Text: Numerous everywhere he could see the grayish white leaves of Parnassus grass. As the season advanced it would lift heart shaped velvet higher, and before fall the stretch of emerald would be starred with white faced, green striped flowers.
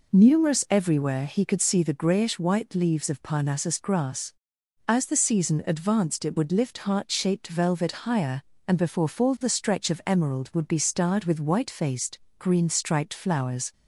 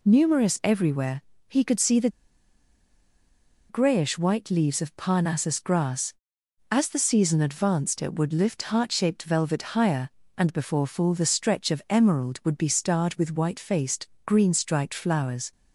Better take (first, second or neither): first